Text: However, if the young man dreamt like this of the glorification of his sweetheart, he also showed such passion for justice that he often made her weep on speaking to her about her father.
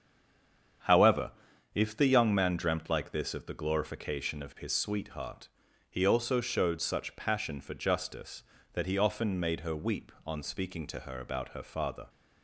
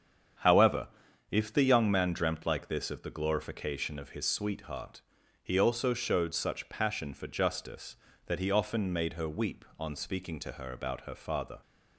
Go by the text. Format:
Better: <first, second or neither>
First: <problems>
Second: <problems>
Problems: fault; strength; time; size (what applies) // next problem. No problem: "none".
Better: second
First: stays silent before the first word; slight; until 0.8 s; 0.8 s long // starts louder than the rest; strong; until 2.3 s; 8 dB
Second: starts louder than the rest; strong; until 1.8 s; 8 dB